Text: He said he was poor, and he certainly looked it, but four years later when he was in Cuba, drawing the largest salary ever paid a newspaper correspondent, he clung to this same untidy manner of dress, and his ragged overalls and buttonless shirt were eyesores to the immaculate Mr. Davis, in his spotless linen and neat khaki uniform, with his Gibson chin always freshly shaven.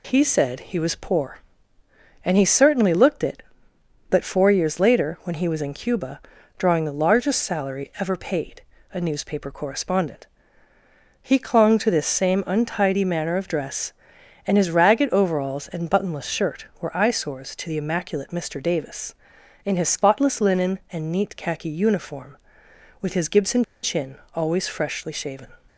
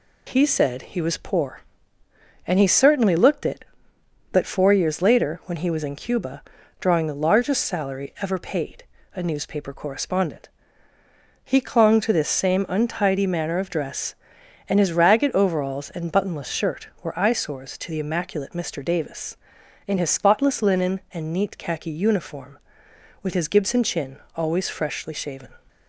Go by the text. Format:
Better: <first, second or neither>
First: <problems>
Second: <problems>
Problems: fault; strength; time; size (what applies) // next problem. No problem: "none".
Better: second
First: pauses between "paid" and "a"; slight; at 8.6 s; 0.32 s long // pauses between "Gibson" and "chin"; slight; at 23.6 s; 0.19 s long // pauses between "chin" and "always"; slight; at 24.1 s; 0.18 s long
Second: pauses between "paid" and "a"; slight; at 8.8 s; 0.32 s long // pauses between "chin" and "always"; slight; at 24.1 s; 0.18 s long